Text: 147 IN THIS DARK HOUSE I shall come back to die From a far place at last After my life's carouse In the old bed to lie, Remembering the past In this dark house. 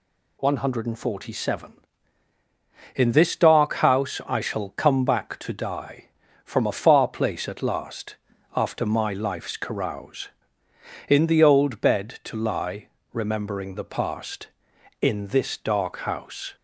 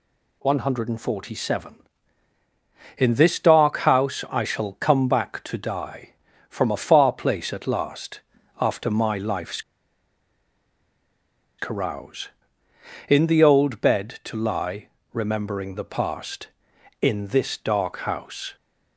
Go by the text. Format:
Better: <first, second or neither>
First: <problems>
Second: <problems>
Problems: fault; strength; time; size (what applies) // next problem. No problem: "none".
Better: first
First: pauses between "last" and "After"; at 8.1 s; 0.38 s long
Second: pauses between "last" and "After"; at 8.1 s; 0.38 s long // pauses between "life's" and "carouse"; strong; at 9.5 s; 1.9 s long